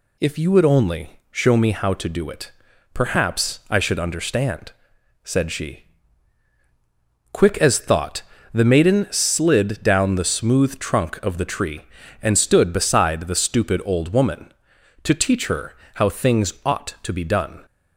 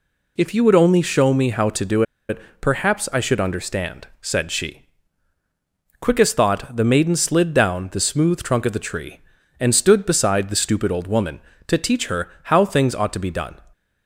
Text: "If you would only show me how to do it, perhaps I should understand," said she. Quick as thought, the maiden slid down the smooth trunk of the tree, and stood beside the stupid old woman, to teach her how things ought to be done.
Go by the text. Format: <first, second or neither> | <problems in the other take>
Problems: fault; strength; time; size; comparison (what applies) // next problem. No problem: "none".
first | pauses between "do" and "it"; slight; at 2.0 s; 0.26 s long // pauses between "her" and "how"; slight; at 12.2 s; 0.16 s long; slight in the first